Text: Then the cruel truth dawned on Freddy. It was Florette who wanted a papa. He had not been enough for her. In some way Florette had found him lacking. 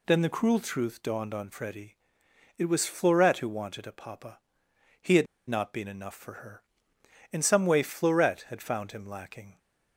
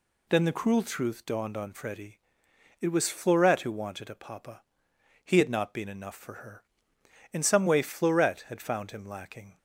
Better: second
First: pauses between "had" and "not"; slight; at 5.2 s; 0.21 s long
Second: none

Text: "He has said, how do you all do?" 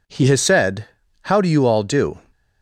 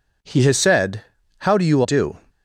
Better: first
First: none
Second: skips "all"; at 1.8 s

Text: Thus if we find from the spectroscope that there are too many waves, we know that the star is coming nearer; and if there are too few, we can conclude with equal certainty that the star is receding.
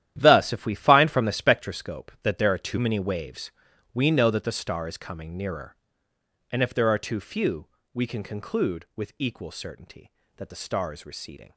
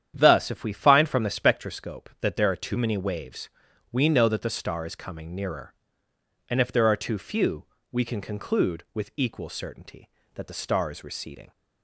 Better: second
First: gets quieter; strong; throughout; 12.5 dB // starts louder than the rest; strong; until 1.1 s; 11.5 dB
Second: starts louder than the rest; strong; until 1.1 s; 9.5 dB

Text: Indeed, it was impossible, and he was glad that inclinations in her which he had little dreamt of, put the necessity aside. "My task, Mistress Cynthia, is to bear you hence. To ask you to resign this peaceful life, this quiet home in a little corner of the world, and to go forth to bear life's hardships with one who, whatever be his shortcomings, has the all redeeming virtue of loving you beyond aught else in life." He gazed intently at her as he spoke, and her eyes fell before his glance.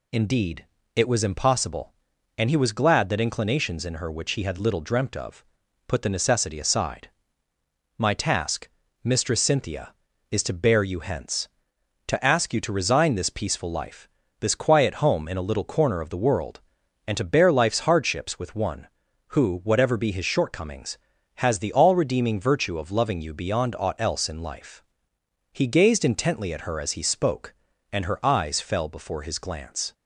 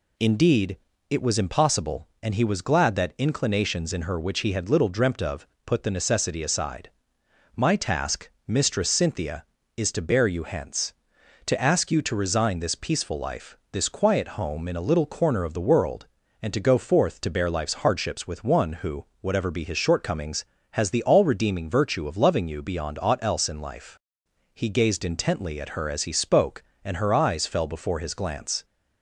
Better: second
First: skips "to go forth"; at 17.1 s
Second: none

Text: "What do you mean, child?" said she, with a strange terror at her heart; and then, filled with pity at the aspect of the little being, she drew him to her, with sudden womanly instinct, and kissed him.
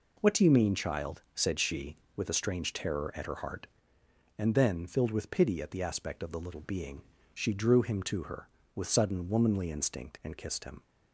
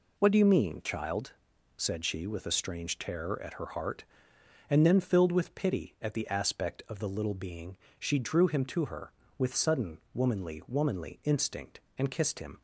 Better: first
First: none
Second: pauses between "sudden" and "womanly"; slight; at 9.9 s; 0.16 s long // says "womanly" twice; at 10.6 s

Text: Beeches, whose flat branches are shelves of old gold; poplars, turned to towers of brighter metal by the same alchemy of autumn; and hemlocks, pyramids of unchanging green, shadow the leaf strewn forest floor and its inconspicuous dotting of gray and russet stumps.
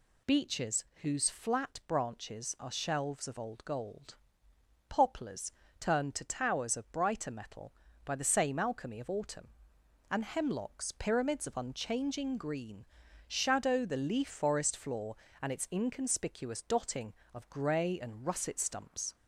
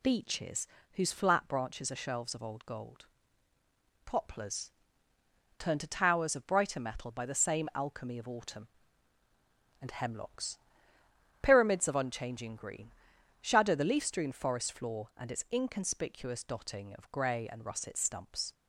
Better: second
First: skips "strewn"; at 14.2 s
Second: none

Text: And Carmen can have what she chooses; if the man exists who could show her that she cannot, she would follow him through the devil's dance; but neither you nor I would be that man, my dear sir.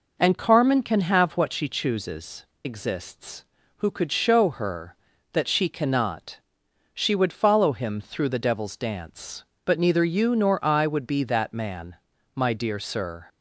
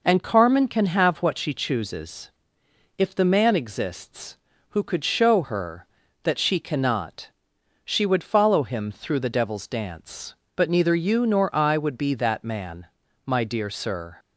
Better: second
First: skips "if the man"; at 2.5 s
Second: none

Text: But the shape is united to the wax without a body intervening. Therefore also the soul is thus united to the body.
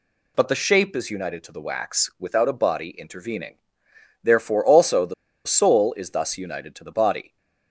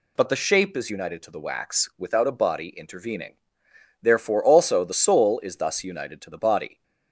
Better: second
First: pauses between "the" and "soul"; slight; at 5.1 s; 0.32 s long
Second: none

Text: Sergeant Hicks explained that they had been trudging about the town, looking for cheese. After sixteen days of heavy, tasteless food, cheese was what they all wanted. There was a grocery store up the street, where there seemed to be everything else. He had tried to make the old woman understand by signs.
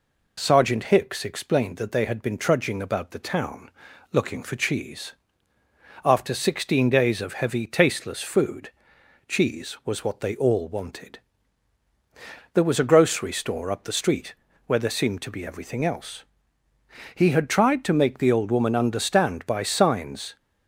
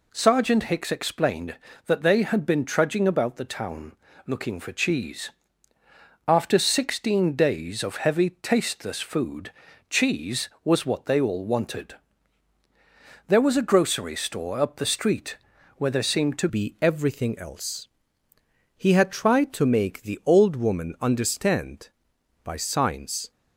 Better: first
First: none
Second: changes voice at "be"; from 16.4 s on; 6.9 s long

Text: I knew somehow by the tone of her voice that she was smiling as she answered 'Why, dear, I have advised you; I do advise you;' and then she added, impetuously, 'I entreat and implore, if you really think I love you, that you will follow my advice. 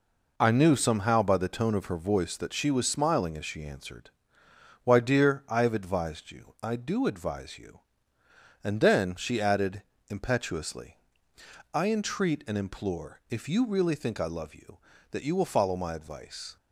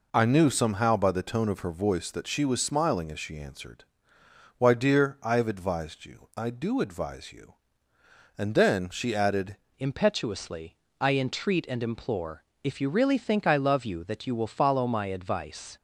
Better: first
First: pauses between "answered" and "Why"; noticeable; at 4.0 s; 0.74 s long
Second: pauses between "answered" and "Why"; noticeable; at 3.8 s; 0.74 s long // changes voice at "impetuously"; from 9.7 s on; 6.0 s long

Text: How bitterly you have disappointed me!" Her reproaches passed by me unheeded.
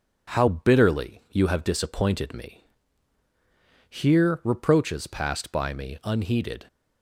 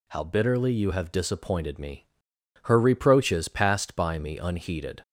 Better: second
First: says "Here" for "Her"; at 3.8 s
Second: none

